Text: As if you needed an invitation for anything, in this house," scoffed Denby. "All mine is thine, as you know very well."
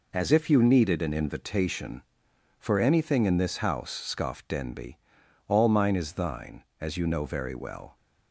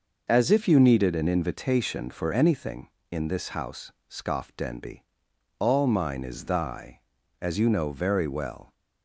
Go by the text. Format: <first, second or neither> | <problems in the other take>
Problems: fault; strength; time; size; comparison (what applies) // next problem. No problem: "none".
first | says "thy" for "thine"; at 6.4 s